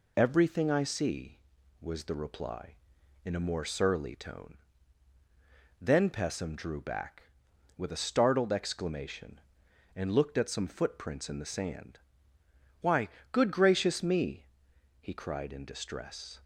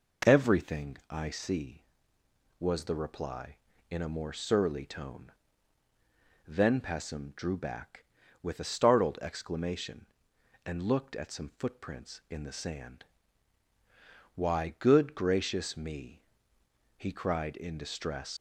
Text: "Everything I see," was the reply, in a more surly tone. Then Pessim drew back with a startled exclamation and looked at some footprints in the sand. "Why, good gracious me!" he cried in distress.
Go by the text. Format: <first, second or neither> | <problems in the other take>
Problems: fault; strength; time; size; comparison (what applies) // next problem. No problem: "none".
first | leaves "distress" unfinished; at 18.3 s; 105 ms